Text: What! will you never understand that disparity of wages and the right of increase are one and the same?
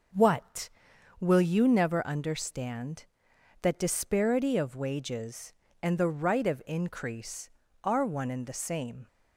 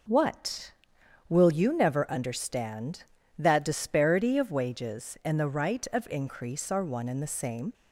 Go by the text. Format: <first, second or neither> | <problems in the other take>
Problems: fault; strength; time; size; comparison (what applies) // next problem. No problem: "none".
neither | none